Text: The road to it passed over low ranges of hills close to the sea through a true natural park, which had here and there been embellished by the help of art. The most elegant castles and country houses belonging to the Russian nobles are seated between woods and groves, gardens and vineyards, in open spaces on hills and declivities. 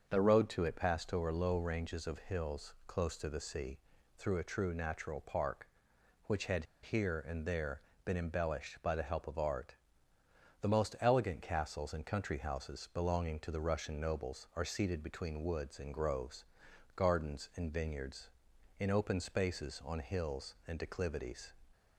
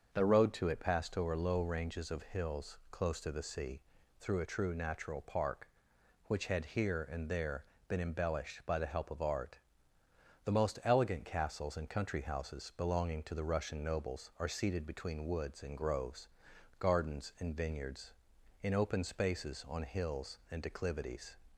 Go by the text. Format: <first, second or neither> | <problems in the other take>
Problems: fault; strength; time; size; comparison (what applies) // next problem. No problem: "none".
second | starts louder than the rest; until 1.1 s; 6.5 dB; also in the second // pauses between "sea" and "through"; at 3.7 s; 0.38 s long; also in the second // pauses between "had" and "here"; slight; at 6.6 s; 0.19 s long // pauses between "there" and "been"; slight; at 7.8 s; 0.22 s long; slight in the second